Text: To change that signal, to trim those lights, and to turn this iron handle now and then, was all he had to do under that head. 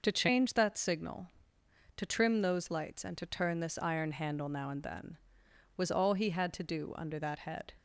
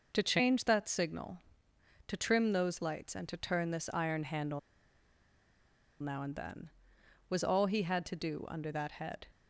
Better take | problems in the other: first | pauses between "handle" and "now"; strong; at 4.5 s; 1.4 s long

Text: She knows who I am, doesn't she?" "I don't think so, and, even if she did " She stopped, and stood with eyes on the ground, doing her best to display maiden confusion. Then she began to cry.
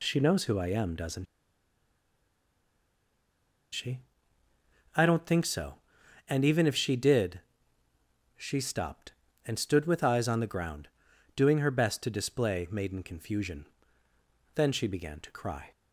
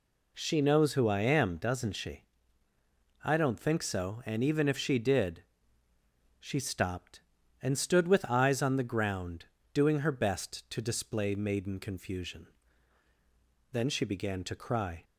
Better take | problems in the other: second | pauses between "doesn't" and "she"; strong; at 1.2 s; 2.4 s long

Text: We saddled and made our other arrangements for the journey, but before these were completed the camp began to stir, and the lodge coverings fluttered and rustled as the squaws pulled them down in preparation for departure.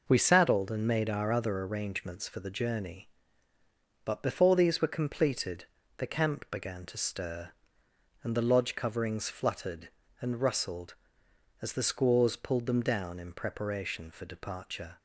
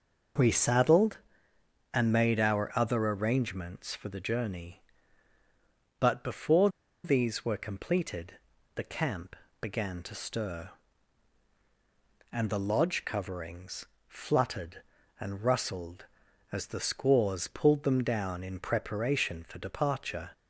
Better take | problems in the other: first | pauses between "before" and "these"; slight; at 6.6 s; 0.35 s long // pauses between "completed" and "the"; at 8.3 s; 0.42 s long; slight in the first // pauses between "camp" and "began"; slight; at 9.3 s; 0.26 s long // pauses between "coverings" and "fluttered"; slight; at 13.8 s; 0.20 s long

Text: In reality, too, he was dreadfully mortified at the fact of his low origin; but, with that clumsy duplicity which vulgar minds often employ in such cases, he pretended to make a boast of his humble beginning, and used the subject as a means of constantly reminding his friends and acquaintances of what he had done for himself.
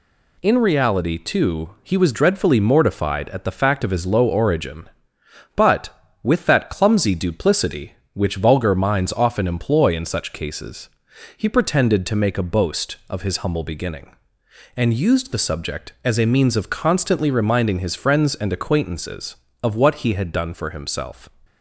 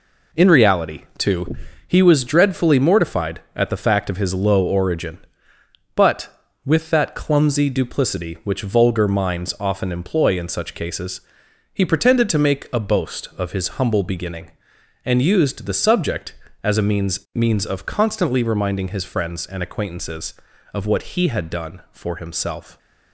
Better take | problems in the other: first | says "means" twice; at 17.3 s

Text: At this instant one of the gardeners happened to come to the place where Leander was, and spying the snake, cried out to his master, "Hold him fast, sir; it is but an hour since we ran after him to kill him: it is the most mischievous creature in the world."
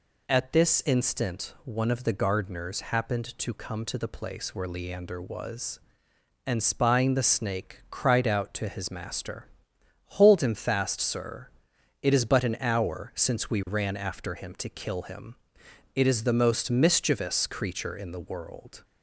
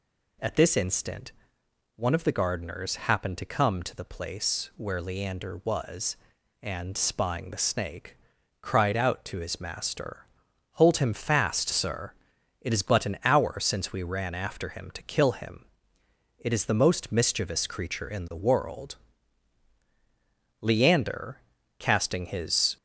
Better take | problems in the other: first | pauses between "instant" and "one"; noticeable; at 1.3 s; 0.64 s long // goes on to say "Leander casting his"; strong; from 20.6 s on; 2.1 s long

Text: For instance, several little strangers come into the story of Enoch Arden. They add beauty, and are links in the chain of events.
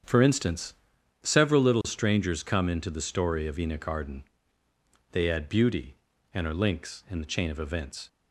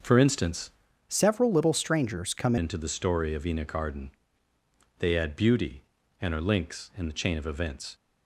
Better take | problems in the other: first | starts louder than the rest; until 1.3 s; 6 dB; strong in the first // changes voice from "several" to "come"; from 1.0 to 2.5 s; 1.5 s long

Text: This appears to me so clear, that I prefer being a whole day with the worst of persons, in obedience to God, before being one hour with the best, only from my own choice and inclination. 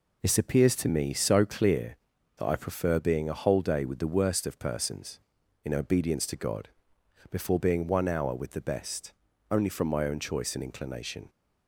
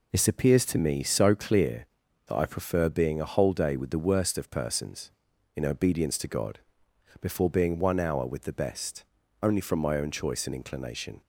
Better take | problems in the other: neither | none

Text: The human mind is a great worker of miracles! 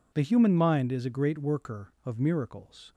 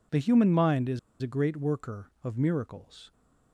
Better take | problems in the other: first | pauses between "is" and "a"; slight; at 0.9 s; 0.22 s long

